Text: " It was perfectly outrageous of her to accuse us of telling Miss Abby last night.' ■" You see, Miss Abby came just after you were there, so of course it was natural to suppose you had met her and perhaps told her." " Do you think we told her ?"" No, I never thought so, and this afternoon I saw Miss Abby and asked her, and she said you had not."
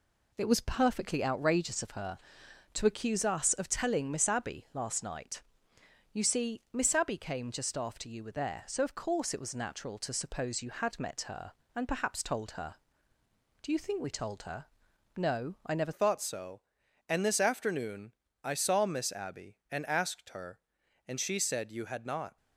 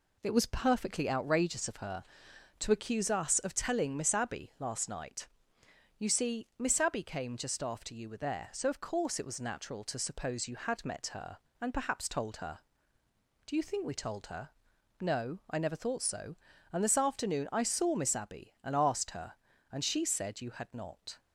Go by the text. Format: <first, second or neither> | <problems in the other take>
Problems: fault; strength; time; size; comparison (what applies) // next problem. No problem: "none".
second | changes voice at "thought"; from 15.9 s on; 6.4 s long // pauses between "afternoon" and "I"; slight; at 18.1 s; 0.32 s long